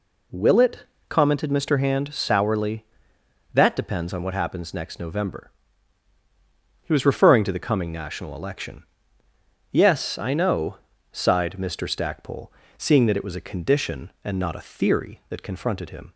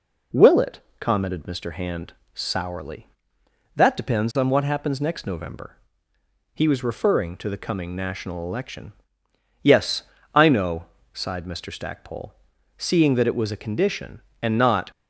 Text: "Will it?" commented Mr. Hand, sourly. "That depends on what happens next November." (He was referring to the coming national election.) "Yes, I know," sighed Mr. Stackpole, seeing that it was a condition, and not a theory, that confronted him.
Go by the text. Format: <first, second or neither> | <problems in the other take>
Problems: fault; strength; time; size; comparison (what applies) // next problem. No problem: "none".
first | stops before "a theory that confronted him"; at 14.9 s